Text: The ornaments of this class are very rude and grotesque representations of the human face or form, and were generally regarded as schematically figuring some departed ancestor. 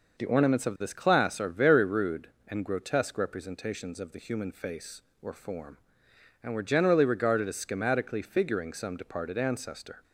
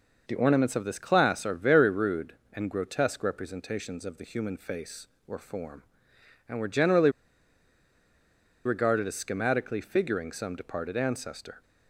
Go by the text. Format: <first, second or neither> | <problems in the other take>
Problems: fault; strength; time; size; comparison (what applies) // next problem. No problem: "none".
first | pauses between "generally" and "regarded"; strong; at 7.1 s; 1.5 s long